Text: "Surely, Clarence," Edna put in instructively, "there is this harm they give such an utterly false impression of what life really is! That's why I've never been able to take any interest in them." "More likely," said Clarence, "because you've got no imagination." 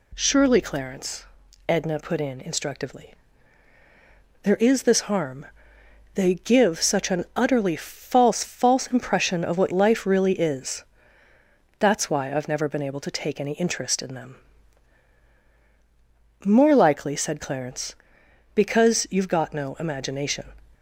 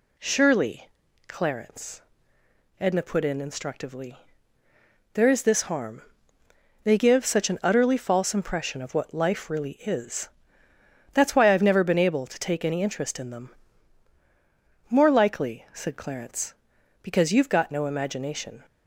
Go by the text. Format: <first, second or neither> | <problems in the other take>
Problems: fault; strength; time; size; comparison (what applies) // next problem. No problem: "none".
second | pauses between "harm" and "they"; noticeable; at 5.4 s; 0.70 s long; noticeable in the second // says "false" twice; at 8.4 s